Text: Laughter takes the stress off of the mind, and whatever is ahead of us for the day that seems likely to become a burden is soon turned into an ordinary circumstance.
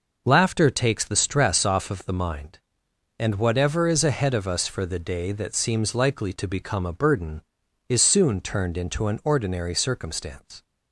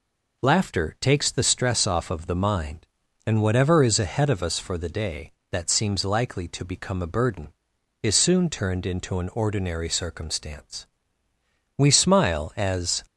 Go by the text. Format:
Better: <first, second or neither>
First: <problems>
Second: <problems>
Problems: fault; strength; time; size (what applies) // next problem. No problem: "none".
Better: first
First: none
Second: goes on to say "We smile as"; noticeable; from 11.7 s on; 1.2 s long